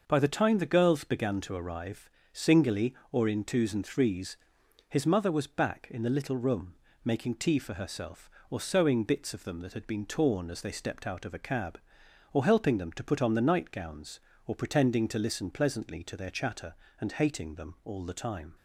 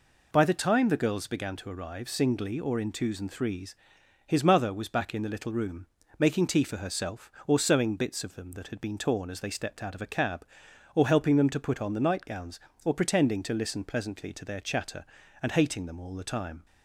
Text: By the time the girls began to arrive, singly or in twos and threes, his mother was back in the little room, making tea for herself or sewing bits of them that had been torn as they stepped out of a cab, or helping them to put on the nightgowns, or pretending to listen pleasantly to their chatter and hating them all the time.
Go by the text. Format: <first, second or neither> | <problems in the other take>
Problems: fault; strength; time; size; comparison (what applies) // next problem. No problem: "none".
neither | none